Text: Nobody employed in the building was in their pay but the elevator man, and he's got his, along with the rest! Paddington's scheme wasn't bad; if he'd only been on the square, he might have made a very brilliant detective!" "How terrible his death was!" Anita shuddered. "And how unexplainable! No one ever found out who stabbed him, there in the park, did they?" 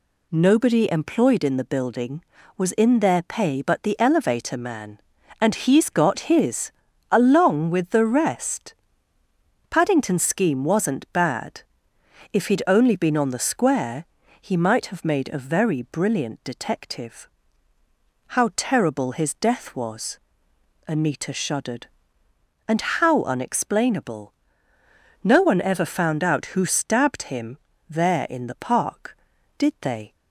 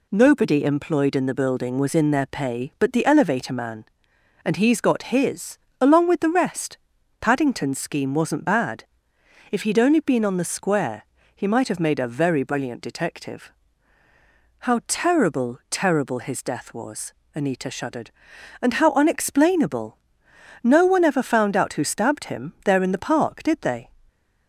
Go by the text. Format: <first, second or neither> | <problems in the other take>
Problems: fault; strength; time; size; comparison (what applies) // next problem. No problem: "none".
first | says "terrible" twice; at 15.7 s